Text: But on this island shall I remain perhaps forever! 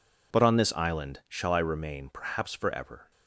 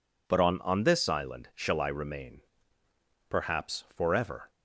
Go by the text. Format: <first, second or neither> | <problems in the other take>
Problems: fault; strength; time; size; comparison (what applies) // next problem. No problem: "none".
first | says "on" twice; at 0.6 s // pauses between "remain" and "perhaps"; noticeable; at 2.4 s; 0.88 s long